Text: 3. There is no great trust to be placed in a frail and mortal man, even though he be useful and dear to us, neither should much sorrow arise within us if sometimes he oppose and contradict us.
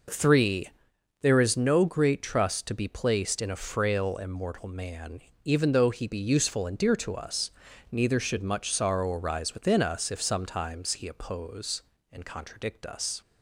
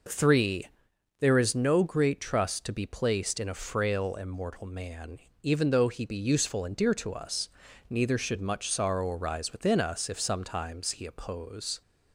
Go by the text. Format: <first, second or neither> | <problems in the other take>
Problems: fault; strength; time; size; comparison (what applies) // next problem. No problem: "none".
first | stops before "and contradict us"; at 11.8 s